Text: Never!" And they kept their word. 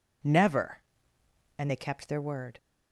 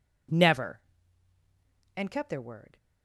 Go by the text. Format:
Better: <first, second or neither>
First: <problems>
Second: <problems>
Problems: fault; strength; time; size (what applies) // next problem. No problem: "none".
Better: first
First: none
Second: skips "they"; at 2.0 s